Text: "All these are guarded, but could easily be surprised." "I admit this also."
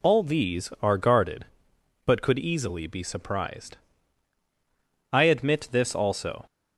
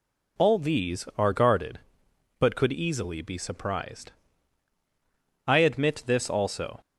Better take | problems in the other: neither | none

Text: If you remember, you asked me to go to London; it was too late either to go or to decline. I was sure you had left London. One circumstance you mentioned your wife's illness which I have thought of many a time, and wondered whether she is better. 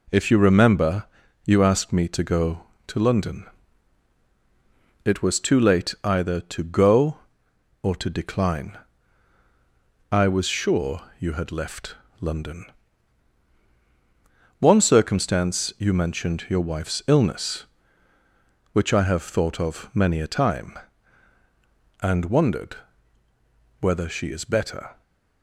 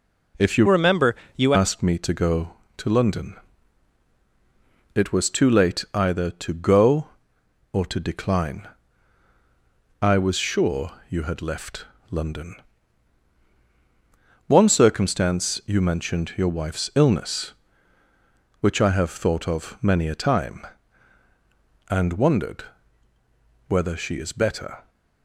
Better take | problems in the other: first | changes voice from "remember" to "you"; from 0.6 to 1.5 s; 0.9 s long // pauses between "sure" and "you"; slight; at 10.9 s; 0.18 s long; slight in the first // pauses between "left" and "London"; slight; at 11.8 s; 0.26 s long; slight in the first // pauses between "wondered" and "whether"; at 22.6 s; 1.0 s long; also in the first

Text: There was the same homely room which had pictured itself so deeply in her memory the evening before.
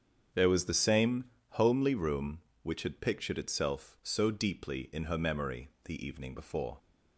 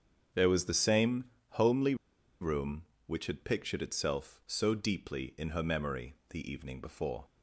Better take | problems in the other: first | starts louder than the rest; strong; until 1.6 s; 8 dB; strong in the first // pauses between "same" and "homely"; slight; at 1.2 s; 0.34 s long; slight in the first // pauses between "homely" and "room"; noticeable; at 1.9 s; 0.46 s long

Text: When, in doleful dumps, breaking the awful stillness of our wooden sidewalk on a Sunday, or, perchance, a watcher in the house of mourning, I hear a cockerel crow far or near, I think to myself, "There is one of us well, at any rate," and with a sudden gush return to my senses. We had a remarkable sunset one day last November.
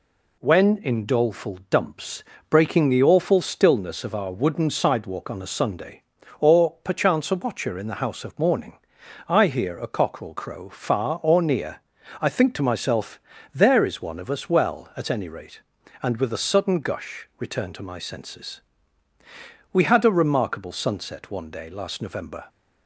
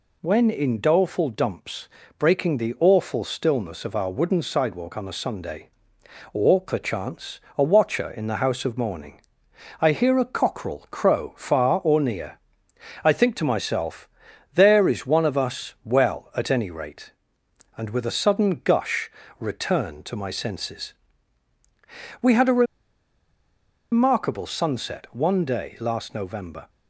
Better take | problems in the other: first | pauses between "gush" and "return"; slight; at 19.1 s; 0.28 s long // pauses between "a" and "remarkable"; strong; at 22.6 s; 1.2 s long

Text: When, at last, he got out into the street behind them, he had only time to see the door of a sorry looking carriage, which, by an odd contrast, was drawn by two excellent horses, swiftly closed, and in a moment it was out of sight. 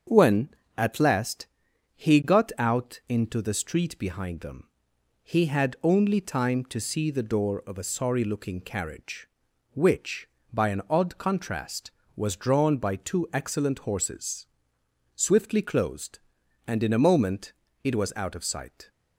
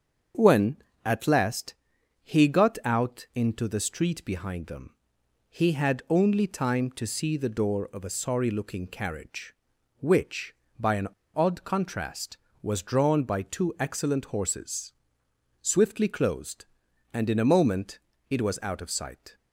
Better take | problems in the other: first | starts louder than the rest; until 1.6 s; 7 dB; also in the first // pauses between "an" and "odd"; slight; at 11.0 s; 0.28 s long // pauses between "moment" and "it"; slight; at 17.9 s; 0.30 s long; slight in the first

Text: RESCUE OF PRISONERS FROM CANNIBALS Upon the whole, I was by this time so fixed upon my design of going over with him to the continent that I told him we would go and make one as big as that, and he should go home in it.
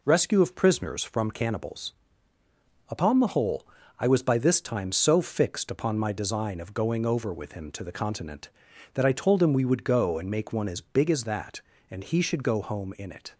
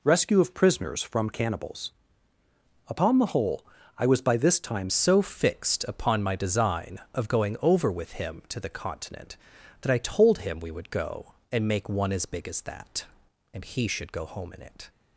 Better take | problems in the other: first | pauses between "CANNIBALS" and "Upon"; noticeable; at 1.9 s; 0.96 s long; noticeable in the first // changes voice at "so"; from 4.8 s on; 10.0 s long

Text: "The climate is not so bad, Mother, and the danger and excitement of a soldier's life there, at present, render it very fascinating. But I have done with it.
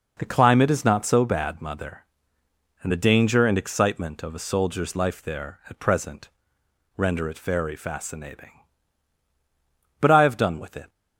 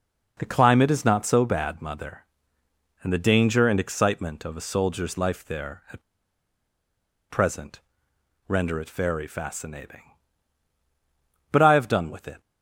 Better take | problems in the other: first | pauses between "at" and "present"; strong; at 6.0 s; 1.3 s long

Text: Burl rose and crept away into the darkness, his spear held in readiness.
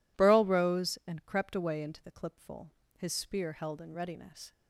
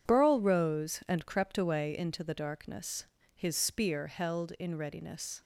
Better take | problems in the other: second | says "clipful" for "darkness"; at 2.1 s

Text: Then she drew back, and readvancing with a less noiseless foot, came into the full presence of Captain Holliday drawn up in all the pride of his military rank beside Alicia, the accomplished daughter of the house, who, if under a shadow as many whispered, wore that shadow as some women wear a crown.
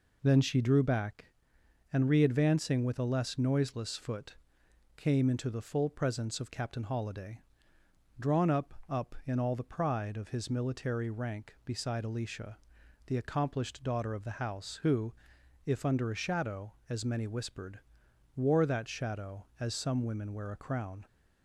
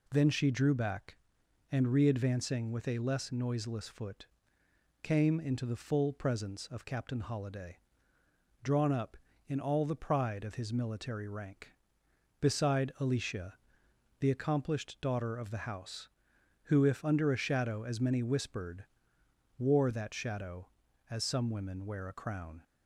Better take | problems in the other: second | pauses between "Holliday" and "drawn"; noticeable; at 7.3 s; 0.80 s long; noticeable in the second // says "up" twice; at 8.8 s

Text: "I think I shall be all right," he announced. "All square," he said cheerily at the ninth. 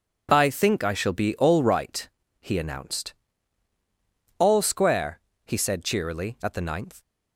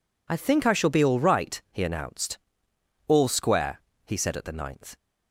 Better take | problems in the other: first | skips "cheerily"; at 4.3 s

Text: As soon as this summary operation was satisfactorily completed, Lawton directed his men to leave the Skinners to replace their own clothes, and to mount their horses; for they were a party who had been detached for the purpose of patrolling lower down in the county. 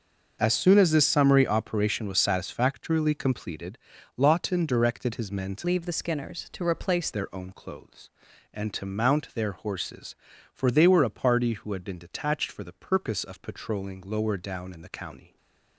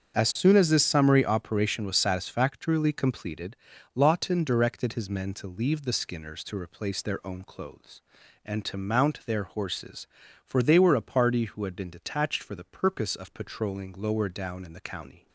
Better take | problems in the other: second | starts louder than the rest; until 1.4 s; 6 dB; also in the second // changes voice from "leave" to "replace"; from 5.6 to 7.0 s; 1.4 s long // stays silent after the last word; slight; from 15.2 s on; 0.5 s long

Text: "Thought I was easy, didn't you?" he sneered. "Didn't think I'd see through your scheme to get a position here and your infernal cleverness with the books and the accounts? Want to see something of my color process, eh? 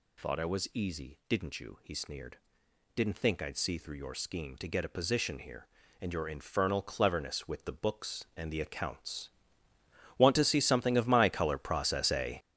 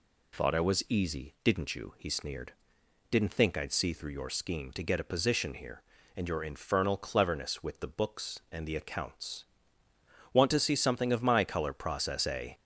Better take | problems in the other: second | gets louder; strong; throughout; 10 dB

